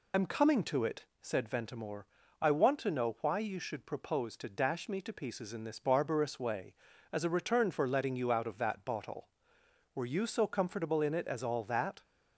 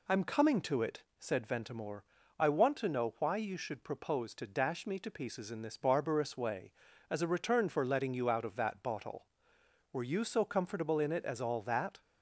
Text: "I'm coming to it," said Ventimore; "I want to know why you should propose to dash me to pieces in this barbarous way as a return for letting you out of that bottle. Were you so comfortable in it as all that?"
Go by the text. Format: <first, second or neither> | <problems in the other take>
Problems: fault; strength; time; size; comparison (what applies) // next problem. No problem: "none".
second | loses the start of "I'm"; at 0.1 s; 40 ms